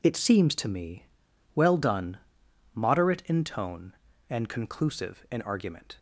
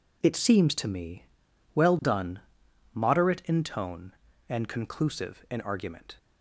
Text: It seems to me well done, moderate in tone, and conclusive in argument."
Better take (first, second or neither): neither